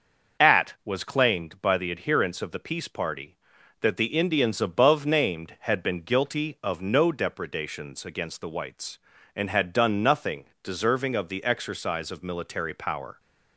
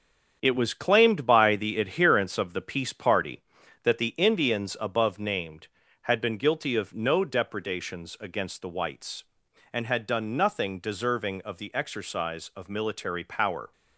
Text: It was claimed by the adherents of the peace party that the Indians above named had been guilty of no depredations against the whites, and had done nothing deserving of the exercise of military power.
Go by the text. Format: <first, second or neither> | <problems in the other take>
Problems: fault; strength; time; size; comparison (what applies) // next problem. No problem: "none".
second | starts louder than the rest; until 1.5 s; 6.5 dB; strong in the second // says "At" for "It"; at 0.3 s // pauses between "nothing" and "deserving"; slight; at 10.4 s; 0.18 s long